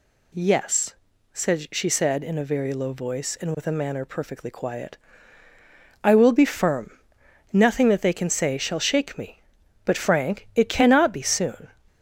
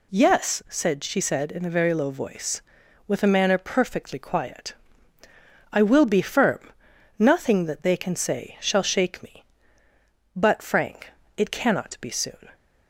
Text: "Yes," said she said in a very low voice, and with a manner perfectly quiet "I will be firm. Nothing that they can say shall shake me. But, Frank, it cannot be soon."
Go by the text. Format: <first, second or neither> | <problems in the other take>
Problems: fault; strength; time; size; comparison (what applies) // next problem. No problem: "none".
first | skips "and"; at 2.8 s // pauses between "quiet" and "I"; noticeable; at 4.7 s; 0.98 s long; also in the first